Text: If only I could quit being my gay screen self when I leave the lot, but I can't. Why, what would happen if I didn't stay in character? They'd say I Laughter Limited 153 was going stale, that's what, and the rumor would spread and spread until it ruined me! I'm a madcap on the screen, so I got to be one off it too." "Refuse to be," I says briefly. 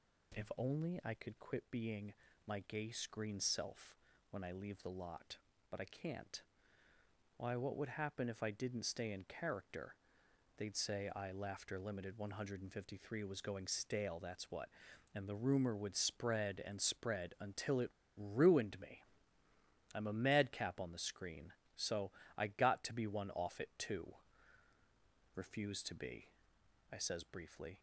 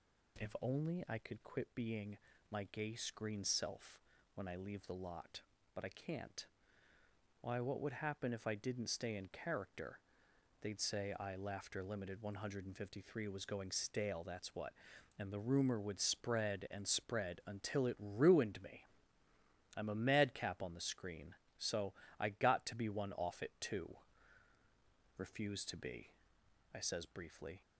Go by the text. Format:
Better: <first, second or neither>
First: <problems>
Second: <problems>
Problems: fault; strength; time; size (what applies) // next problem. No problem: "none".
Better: second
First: pauses between "being" and "my"; slight; at 2.1 s; 0.34 s long // pauses between "self" and "when"; slight; at 3.9 s; 0.34 s long // pauses between "it" and "ruined"; slight; at 17.8 s; 0.28 s long // pauses between "so" and "I"; slight; at 22.1 s; 0.26 s long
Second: pauses between "being" and "my"; slight; at 2.1 s; 0.34 s long // pauses between "self" and "when"; slight; at 4.0 s; 0.34 s long // pauses between "so" and "I"; slight; at 21.9 s; 0.26 s long